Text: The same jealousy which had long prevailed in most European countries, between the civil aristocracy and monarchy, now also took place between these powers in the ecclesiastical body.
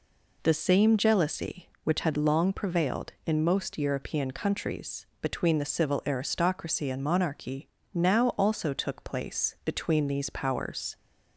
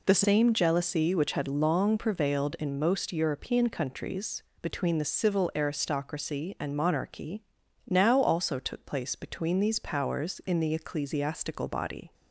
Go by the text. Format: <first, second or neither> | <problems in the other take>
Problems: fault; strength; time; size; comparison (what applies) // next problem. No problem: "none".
second | stops before "in the ecclesiastical body"; at 10.9 s